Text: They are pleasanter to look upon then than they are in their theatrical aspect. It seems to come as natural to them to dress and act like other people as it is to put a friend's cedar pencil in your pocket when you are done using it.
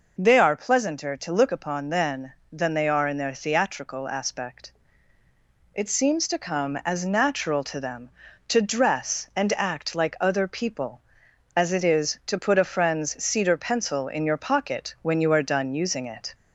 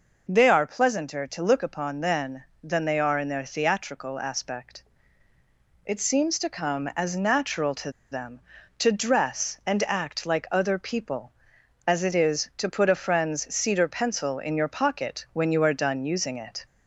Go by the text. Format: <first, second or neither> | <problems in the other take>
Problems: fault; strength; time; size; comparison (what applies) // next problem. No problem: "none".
first | pauses between "to" and "them"; slight; at 7.9 s; 0.19 s long